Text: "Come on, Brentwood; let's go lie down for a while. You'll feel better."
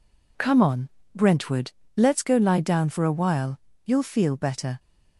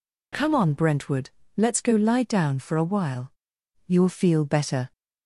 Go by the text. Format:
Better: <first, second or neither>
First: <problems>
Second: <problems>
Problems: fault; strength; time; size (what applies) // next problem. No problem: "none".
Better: neither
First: none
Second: none